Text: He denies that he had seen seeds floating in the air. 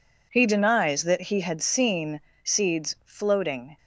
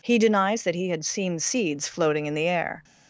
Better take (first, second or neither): second